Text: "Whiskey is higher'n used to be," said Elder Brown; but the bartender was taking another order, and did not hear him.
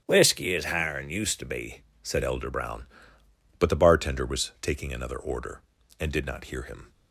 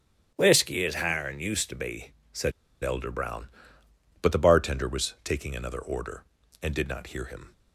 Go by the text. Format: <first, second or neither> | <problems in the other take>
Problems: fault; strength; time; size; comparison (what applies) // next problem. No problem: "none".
first | starts louder than the rest; strong; until 1.3 s; 10 dB; strong in the first // pauses between "said" and "Elder"; slight; at 2.5 s; 0.32 s long